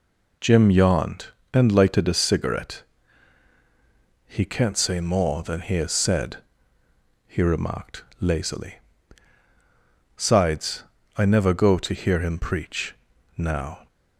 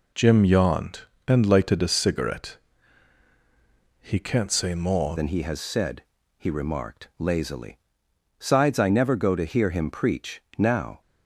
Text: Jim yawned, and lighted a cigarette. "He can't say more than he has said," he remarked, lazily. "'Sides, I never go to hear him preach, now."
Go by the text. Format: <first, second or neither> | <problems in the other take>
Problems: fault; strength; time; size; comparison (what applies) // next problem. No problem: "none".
first | changes voice at "than"; from 5.1 s on; 5.9 s long